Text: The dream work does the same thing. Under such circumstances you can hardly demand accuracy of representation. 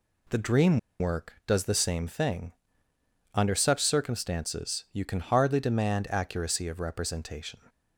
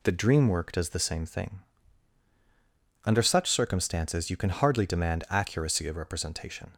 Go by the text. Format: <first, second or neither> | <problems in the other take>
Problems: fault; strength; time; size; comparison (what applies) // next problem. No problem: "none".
second | pauses between "dream" and "work"; slight; at 0.7 s; 0.20 s long